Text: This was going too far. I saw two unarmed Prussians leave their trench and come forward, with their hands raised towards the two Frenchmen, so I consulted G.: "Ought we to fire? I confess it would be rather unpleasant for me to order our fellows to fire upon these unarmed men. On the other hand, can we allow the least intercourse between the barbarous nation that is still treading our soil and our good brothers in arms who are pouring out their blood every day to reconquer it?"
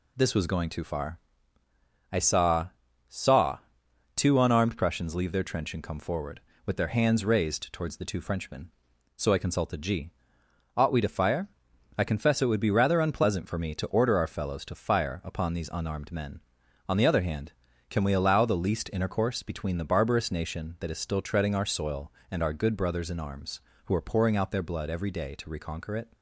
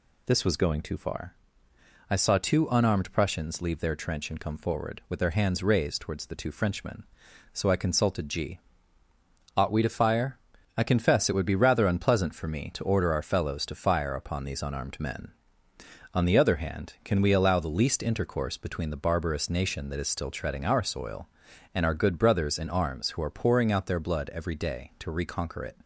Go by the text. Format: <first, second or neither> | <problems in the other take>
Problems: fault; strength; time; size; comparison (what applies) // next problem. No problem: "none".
second | says "saw" twice; at 3.0 s